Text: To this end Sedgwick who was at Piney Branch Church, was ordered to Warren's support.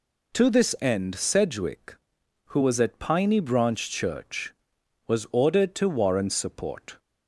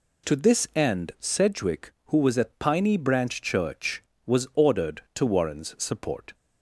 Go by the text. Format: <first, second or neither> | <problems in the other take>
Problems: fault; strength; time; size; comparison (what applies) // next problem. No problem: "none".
neither | none